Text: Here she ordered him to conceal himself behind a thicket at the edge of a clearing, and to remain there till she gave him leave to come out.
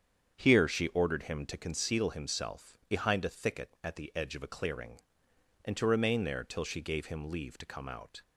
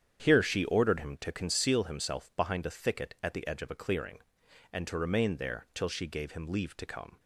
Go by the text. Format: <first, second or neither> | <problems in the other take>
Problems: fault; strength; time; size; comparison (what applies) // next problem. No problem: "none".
first | starts louder than the rest; strong; until 1.2 s; 8.5 dB; strong in the first // stops before "out"; at 7.1 s